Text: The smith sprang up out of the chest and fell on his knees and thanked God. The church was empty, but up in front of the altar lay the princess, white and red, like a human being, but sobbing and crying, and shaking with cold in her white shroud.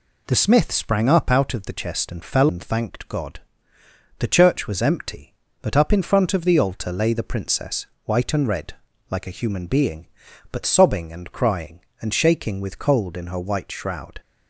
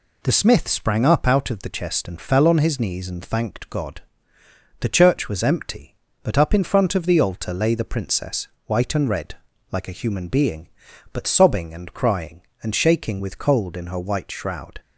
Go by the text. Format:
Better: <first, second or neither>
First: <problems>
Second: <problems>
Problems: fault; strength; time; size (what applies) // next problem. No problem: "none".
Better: second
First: skips "on his knees"; at 2.4 s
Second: none